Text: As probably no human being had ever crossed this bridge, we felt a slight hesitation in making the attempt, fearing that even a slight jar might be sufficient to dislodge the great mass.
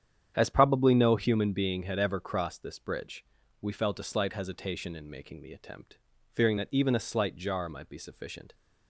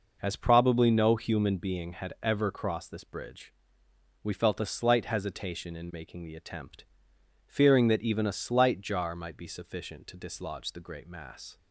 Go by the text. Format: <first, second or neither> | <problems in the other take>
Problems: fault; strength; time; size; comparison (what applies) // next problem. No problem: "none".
second | starts louder than the rest; strong; until 1.3 s; 9 dB // stops before "to dislodge the great mass"; at 8.5 s